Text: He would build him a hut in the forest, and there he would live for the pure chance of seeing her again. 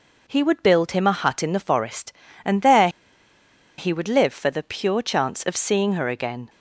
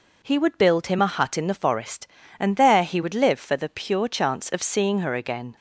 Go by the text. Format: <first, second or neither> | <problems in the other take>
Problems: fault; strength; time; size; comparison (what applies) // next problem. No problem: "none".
second | pauses between "there" and "he"; noticeable; at 2.8 s; 0.89 s long